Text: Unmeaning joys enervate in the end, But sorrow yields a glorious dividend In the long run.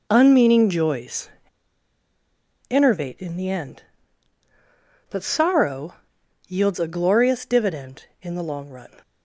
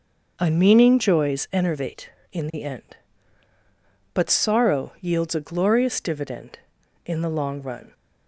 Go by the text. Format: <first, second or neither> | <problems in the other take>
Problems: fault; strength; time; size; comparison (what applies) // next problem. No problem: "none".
second | pauses between "joys" and "enervate"; strong; at 1.2 s; 1.4 s long // pauses between "sorrow" and "yields"; noticeable; at 5.9 s; 0.50 s long